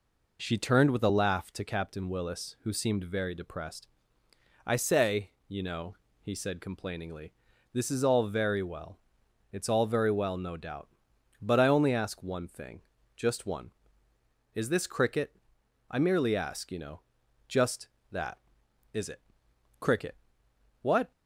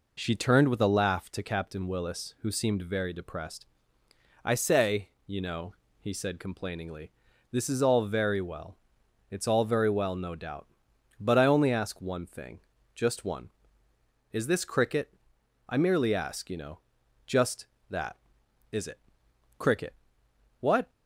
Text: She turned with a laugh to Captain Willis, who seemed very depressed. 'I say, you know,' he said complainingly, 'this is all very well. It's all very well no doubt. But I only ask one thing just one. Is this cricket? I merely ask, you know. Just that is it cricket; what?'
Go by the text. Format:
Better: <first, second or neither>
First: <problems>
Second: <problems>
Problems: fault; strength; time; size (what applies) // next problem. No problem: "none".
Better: neither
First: pauses between "thing" and "just"; at 12.7 s; 0.38 s long // pauses between "it" and "cricket"; noticeable; at 19.1 s; 0.62 s long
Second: pauses between "thing" and "just"; at 12.5 s; 0.38 s long // pauses between "it" and "cricket"; noticeable; at 18.9 s; 0.62 s long